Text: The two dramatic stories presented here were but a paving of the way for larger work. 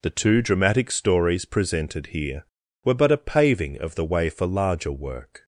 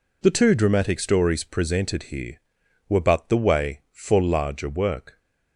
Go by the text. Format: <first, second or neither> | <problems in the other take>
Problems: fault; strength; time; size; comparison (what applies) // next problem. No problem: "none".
first | skips "a paving of"; at 3.2 s